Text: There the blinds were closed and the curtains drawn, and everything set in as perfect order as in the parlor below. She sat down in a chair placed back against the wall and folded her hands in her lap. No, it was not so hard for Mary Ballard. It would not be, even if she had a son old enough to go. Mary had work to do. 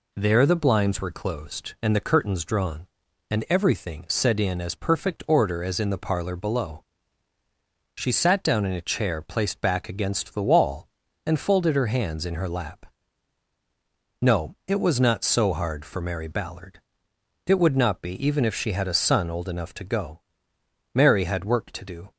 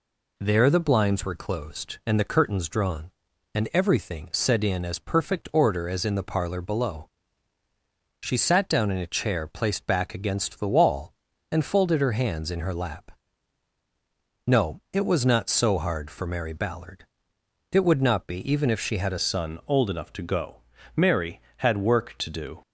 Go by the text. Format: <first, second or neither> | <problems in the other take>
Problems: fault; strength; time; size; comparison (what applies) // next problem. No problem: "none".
first | changes voice at "son"; from 19.1 s on; 3.5 s long